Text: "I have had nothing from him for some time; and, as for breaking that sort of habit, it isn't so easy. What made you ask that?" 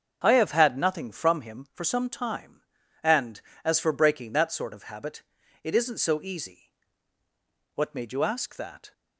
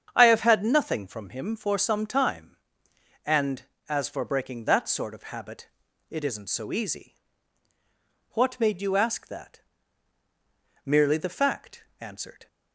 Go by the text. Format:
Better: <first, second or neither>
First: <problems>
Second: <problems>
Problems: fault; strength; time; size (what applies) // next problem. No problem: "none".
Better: first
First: starts louder than the rest; until 1.2 s; 7 dB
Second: starts louder than the rest; strong; until 1.1 s; 8 dB // goes on to say "Merely the fact answered"; from 10.8 s on; 1.6 s long